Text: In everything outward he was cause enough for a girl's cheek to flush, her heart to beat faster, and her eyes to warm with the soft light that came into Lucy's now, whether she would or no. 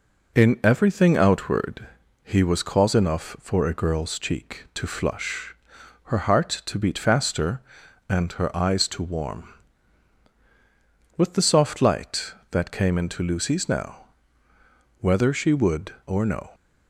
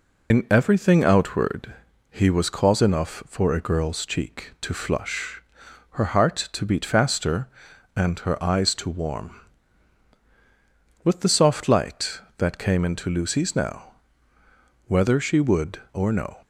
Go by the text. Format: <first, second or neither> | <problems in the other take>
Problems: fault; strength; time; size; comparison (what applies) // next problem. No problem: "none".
first | loses the start of "In"; at 0.3 s; 80 ms // pauses between "outward" and "he"; at 1.7 s; 0.38 s long; also in the first